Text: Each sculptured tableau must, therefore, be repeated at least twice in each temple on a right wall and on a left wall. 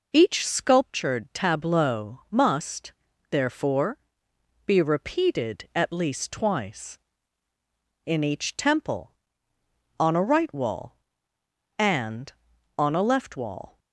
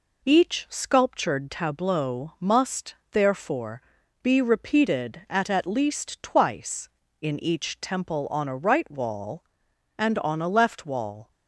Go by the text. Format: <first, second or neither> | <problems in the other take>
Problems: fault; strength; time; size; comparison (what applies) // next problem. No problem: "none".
first | says "at" twice; at 5.5 s